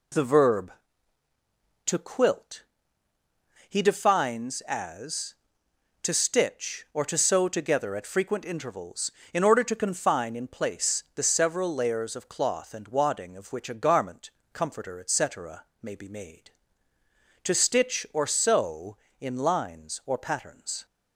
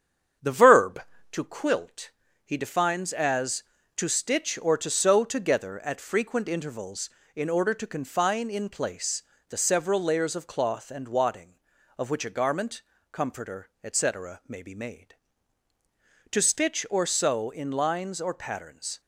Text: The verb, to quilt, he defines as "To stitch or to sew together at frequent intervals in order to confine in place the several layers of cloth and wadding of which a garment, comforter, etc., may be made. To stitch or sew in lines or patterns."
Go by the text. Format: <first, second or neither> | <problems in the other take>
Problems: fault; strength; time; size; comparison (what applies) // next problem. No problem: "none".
first | starts louder than the rest; strong; until 1.4 s; 8.5 dB // pauses between "place" and "the"; slight; at 9.2 s; 0.24 s long